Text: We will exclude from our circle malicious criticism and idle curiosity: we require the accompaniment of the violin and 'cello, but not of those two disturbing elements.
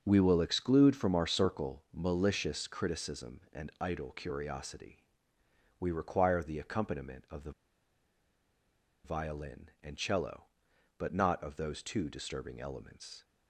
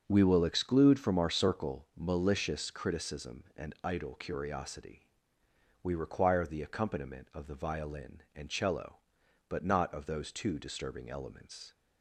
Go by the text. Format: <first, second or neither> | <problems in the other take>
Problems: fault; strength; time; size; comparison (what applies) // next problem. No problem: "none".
second | starts louder than the rest; noticeable; until 1.0 s; 6 dB; also in the second // pauses between "the" and "violin"; strong; at 7.5 s; 1.5 s long